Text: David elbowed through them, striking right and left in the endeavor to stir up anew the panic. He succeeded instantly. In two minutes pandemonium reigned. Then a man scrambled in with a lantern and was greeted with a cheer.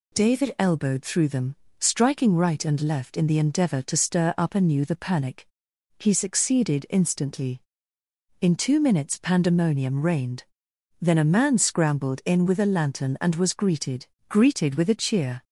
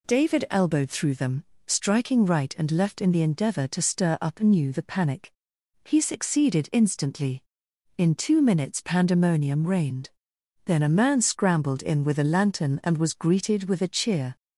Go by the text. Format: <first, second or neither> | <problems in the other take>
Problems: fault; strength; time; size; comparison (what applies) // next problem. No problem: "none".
second | says "greeted" twice; at 14.2 s